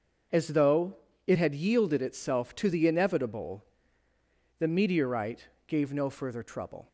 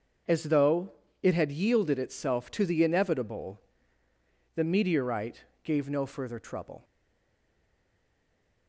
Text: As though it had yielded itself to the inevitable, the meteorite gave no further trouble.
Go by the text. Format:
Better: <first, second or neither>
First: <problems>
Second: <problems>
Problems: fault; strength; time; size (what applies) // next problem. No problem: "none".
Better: first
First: starts louder than the rest; until 1.6 s; 6.5 dB // pauses between "though" and "it"; slight; at 0.9 s; 0.30 s long // pauses between "meteorite" and "gave"; slight; at 5.4 s; 0.20 s long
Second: starts louder than the rest; until 1.5 s; 6.5 dB // pauses between "though" and "it"; slight; at 0.9 s; 0.30 s long // pauses between "meteorite" and "gave"; slight; at 5.4 s; 0.20 s long // stays silent after the last word; noticeable; from 6.8 s on; 1.8 s long